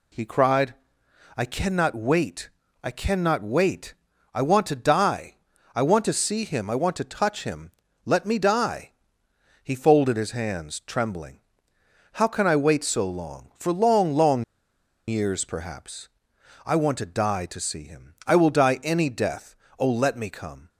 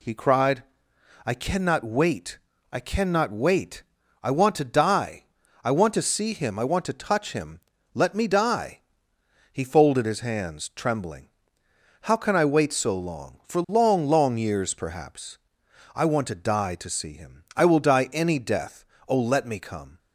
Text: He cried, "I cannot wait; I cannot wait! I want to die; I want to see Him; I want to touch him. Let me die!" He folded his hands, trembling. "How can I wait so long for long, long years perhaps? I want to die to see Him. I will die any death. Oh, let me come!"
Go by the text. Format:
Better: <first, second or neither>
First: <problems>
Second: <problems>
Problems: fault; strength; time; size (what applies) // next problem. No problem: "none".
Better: second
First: pauses between "long" and "years"; noticeable; at 14.4 s; 0.64 s long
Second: none